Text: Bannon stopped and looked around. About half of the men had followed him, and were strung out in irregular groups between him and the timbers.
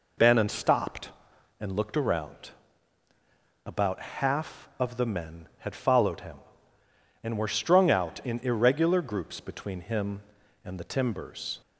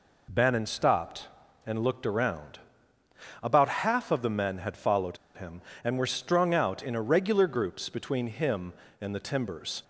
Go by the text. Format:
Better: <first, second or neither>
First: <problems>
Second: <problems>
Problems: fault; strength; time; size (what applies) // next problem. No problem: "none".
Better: first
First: none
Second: pauses between "followed" and "him"; slight; at 5.1 s; 0.18 s long